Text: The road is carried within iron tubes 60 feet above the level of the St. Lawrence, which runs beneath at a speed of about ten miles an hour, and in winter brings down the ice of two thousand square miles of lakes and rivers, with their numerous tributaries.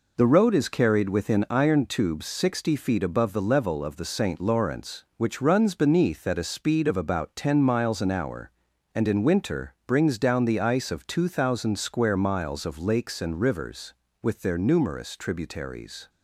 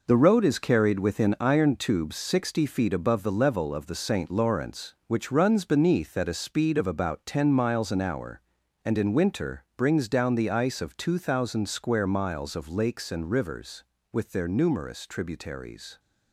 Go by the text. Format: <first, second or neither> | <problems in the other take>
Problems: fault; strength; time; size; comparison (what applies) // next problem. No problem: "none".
first | gets quieter; strong; throughout; 8 dB